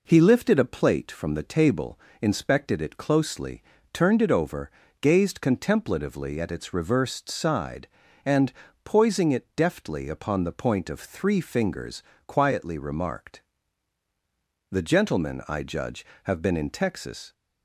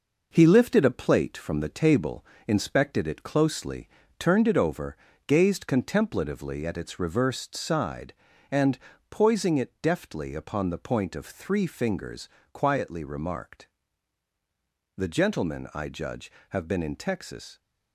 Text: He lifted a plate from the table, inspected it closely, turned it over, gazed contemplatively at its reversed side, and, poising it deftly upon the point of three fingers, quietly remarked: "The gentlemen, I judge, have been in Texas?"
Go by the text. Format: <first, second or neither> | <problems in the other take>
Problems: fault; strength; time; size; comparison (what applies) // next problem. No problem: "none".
first | gets quieter; noticeable; throughout; 5.5 dB